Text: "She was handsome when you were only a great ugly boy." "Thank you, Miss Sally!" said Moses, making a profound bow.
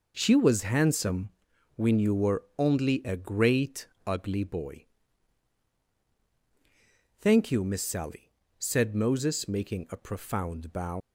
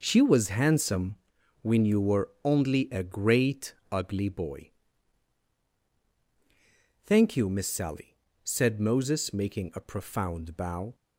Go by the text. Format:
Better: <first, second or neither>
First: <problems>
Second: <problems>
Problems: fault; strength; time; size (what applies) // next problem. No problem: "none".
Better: second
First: pauses between "handsome" and "when"; noticeable; at 1.2 s; 0.48 s long // pauses between "great" and "ugly"; slight; at 3.8 s; 0.18 s long // leaves "bow" unfinished; at 11.0 s; 105 ms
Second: pauses between "handsome" and "when"; noticeable; at 1.1 s; 0.48 s long // pauses between "great" and "ugly"; slight; at 3.7 s; 0.16 s long